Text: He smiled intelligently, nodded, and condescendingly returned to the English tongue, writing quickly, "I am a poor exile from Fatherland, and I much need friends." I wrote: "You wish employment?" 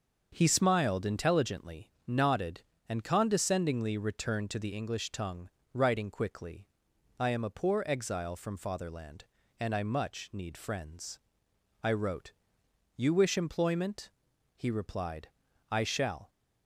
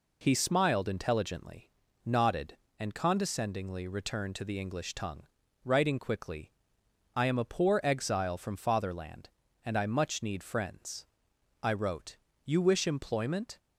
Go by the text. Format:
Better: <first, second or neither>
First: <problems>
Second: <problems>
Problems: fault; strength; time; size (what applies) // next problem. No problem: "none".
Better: second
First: starts louder than the rest; until 1.3 s; 6.5 dB // goes on to say "He replied I shall"; strong; from 14.5 s on; 1.7 s long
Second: none